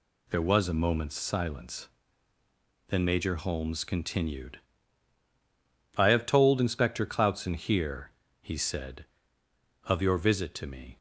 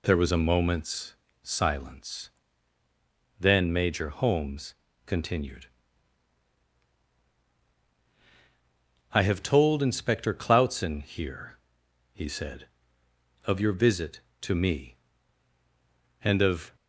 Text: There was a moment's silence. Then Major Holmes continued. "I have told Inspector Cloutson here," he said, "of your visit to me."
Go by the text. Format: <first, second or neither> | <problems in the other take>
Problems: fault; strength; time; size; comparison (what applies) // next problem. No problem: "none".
first | pauses between "moment's" and "silence"; slight; at 1.1 s; 0.26 s long // pauses between "Holmes" and "continued"; slight; at 4.7 s; 0.32 s long // goes on to say "And of"; from 16.2 s on; 0.54 s long